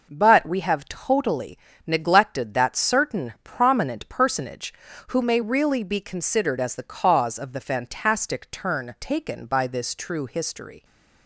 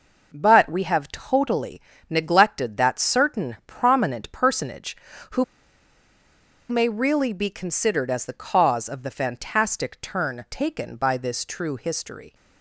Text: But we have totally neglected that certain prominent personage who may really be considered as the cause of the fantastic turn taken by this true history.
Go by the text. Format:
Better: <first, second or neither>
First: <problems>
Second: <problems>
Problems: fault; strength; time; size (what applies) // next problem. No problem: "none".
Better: first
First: pauses between "totally" and "neglected"; slight; at 1.5 s; 0.30 s long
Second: pauses between "totally" and "neglected"; slight; at 1.7 s; 0.30 s long // pauses between "who" and "may"; strong; at 5.4 s; 1.2 s long